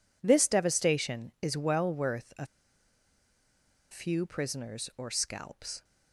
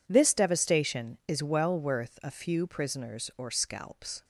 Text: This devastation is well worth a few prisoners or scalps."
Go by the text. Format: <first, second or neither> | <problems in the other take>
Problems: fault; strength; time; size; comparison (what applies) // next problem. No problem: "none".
second | pauses between "a" and "few"; strong; at 2.4 s; 1.4 s long